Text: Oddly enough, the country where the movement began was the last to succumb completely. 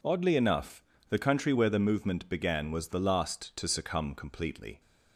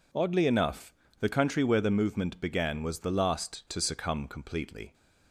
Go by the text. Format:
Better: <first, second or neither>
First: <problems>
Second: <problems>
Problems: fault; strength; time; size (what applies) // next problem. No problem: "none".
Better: neither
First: none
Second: none